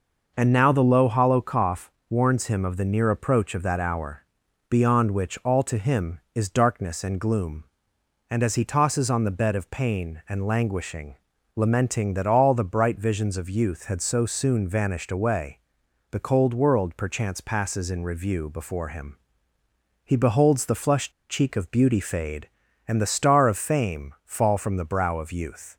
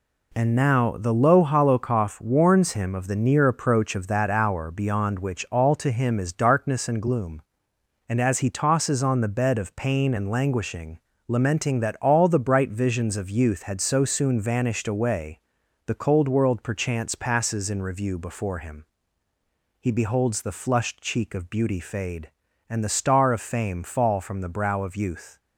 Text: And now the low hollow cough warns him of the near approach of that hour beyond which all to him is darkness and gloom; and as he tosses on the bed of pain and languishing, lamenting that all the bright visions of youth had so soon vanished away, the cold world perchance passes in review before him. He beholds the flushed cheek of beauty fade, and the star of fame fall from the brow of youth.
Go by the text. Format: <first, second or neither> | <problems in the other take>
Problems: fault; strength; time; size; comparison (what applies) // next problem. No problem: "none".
second | pauses between "cough" and "warns"; slight; at 1.9 s; 0.18 s long // pauses between "hour" and "beyond"; noticeable; at 4.1 s; 0.50 s long // pauses between "flushed" and "cheek"; slight; at 21.1 s; 0.18 s long